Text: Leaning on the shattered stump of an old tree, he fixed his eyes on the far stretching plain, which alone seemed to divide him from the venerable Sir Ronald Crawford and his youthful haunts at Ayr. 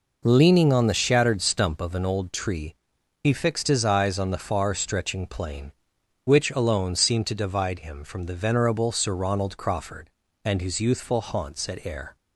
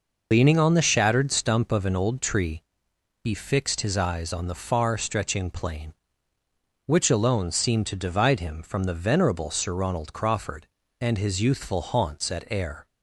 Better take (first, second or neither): first